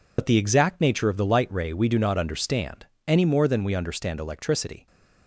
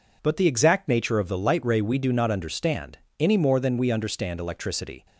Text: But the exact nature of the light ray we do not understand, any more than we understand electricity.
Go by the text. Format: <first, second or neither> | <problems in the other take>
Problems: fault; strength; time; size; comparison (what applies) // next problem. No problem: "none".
second | loses the start of "But"; at 0.1 s; 70 ms